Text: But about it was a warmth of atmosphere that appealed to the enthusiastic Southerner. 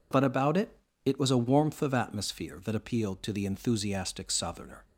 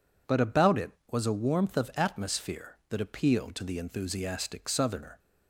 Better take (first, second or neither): second